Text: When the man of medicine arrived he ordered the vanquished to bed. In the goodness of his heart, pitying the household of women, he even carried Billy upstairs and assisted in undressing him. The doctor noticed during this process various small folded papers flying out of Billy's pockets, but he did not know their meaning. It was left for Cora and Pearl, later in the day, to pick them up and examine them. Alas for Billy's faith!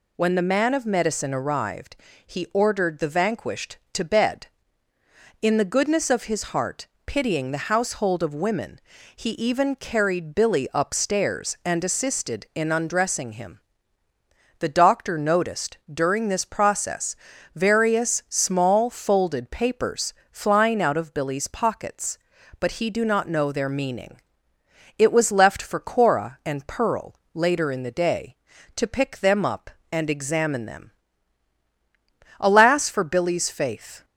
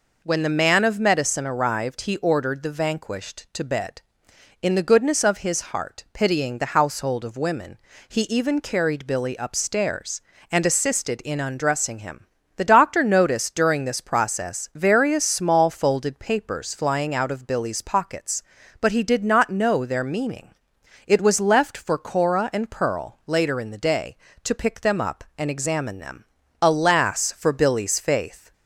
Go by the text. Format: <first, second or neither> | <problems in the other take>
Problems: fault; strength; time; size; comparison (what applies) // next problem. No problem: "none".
second | pauses between "arrived" and "he"; slight; at 1.9 s; 0.28 s long // pauses between "process" and "various"; at 17.1 s; 0.38 s long // pauses between "papers" and "flying"; slight; at 20.1 s; 0.18 s long // says "do" for "did"; at 22.8 s